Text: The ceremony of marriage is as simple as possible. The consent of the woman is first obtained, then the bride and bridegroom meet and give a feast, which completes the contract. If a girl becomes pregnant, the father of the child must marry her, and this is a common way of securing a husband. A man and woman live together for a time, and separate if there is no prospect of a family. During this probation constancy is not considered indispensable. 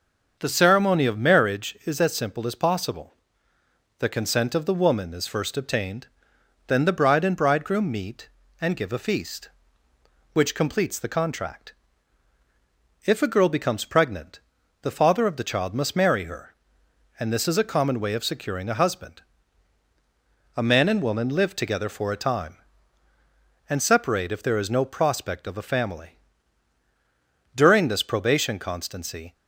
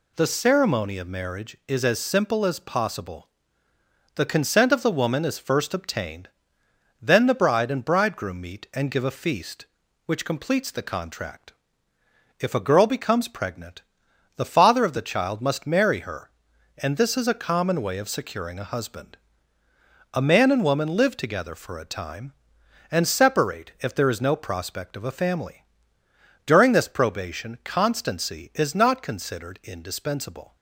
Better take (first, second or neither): second